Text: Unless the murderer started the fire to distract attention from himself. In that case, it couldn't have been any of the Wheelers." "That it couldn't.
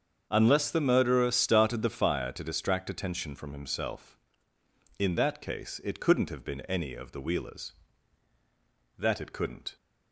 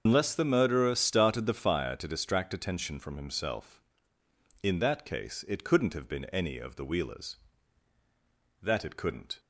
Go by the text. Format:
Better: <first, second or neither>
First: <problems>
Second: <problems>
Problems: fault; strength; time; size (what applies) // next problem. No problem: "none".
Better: first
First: starts louder than the rest; until 1.3 s; 7 dB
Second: loses the start of "Unless"; at 0.0 s; 115 ms // starts louder than the rest; until 1.0 s; 6.5 dB